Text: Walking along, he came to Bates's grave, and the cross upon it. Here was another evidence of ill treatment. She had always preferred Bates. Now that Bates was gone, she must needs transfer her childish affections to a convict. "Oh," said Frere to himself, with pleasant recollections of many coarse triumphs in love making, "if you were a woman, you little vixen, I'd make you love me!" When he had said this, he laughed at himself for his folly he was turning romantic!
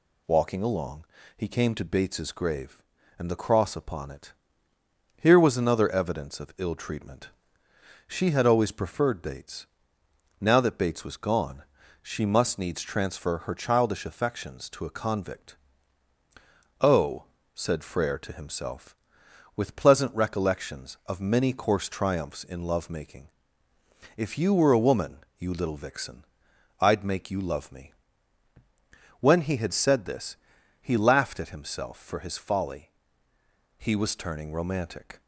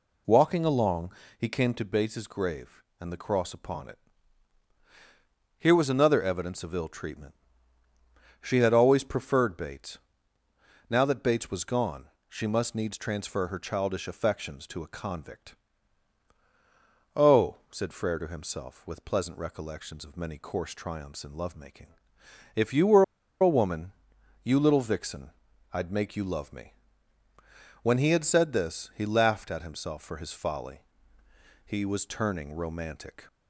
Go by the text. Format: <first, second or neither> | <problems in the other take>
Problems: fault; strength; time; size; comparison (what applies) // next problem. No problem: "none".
first | pauses between "were" and "a"; at 23.0 s; 0.37 s long // pauses between "folly" and "he"; noticeable; at 30.8 s; 0.84 s long; noticeable in the first